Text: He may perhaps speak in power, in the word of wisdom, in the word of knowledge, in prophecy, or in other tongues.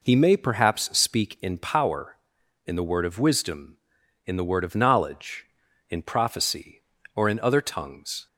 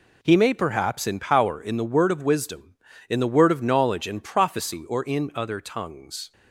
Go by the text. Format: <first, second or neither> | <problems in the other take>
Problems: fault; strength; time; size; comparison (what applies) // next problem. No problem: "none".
first | skips "speak"; at 1.0 s